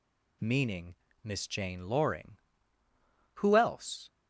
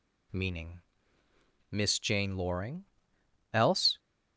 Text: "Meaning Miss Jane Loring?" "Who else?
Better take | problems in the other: first | pauses between "Meaning" and "Miss"; noticeable; at 0.8 s; 0.92 s long; slight in the first // skips "Who"; at 3.1 s

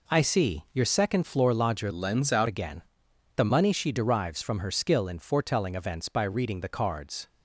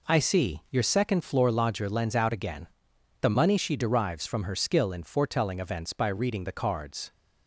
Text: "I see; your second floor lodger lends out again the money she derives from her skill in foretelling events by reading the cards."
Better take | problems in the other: second | changes voice from "lends" to "out"; from 1.9 to 2.4 s; 0.5 s long // pauses between "again" and "the"; noticeable; at 2.8 s; 0.54 s long; noticeable in the second

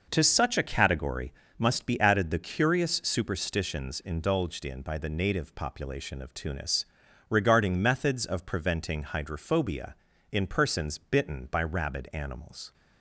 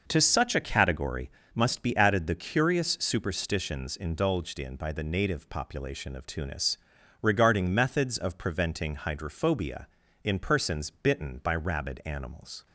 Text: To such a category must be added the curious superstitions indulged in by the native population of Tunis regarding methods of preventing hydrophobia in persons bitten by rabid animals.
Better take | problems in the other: neither | pauses between "category" and "must"; slight; the same in both // pauses between "Tunis" and "regarding"; the same in both

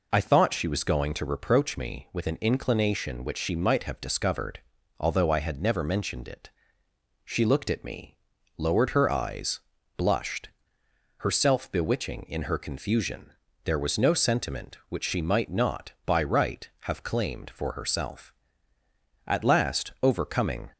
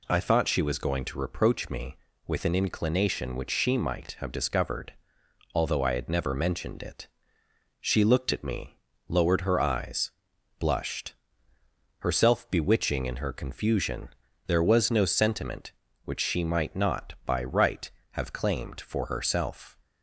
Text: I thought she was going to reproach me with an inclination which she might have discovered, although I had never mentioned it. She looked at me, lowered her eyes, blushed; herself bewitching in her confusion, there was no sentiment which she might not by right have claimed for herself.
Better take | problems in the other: second | goes on to say "At last overcoming"; from 19.2 s on; 1.4 s long

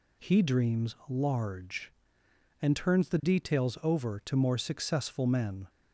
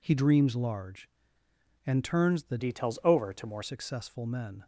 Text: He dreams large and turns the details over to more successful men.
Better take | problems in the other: first | changes voice from "details" to "more"; from 2.5 to 3.6 s; 1.1 s long

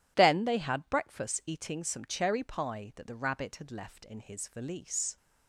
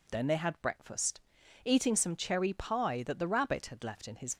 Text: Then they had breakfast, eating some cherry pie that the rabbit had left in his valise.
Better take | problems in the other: first | stops before "valise"; at 4.3 s

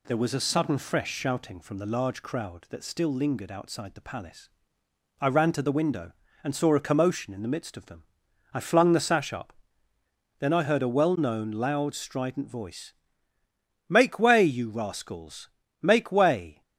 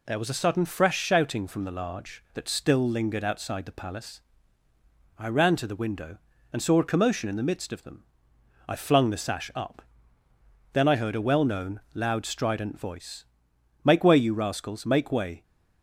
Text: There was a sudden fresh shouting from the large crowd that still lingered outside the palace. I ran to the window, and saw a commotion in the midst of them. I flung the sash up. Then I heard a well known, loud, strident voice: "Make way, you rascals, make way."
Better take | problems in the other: first | skips "crowd"; at 2.2 s

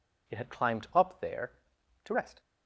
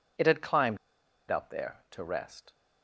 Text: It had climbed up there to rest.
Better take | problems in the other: first | pauses between "climbed" and "up"; noticeable; at 0.7 s; 0.52 s long

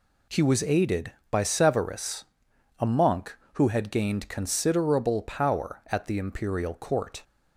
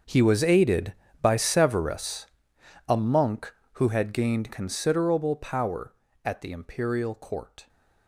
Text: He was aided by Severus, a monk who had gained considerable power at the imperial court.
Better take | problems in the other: first | gets quieter; strong; throughout; 16.5 dB

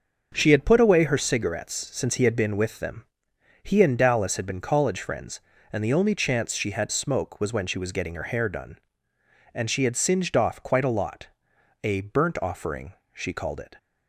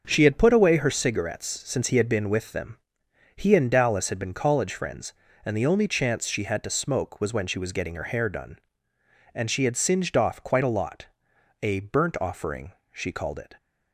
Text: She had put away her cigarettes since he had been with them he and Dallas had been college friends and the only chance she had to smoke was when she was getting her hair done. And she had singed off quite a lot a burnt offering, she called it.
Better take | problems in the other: second | starts louder than the rest; until 1.3 s; 6.5 dB; also in the second // pauses between "them" and "he"; noticeable; at 3.0 s; 0.60 s long; noticeable in the second // skips "to"; at 6.8 s // pauses between "lot" and "a"; noticeable; at 11.2 s; 0.54 s long; noticeable in the second

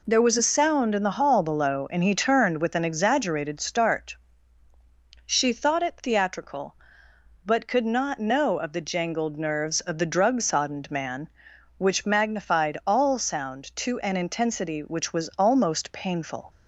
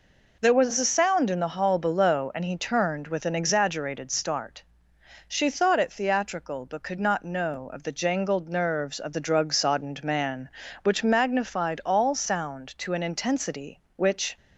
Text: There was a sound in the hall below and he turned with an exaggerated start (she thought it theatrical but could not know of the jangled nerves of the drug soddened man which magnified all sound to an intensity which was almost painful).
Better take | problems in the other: first | stops before "was almost painful"; at 14.3 s

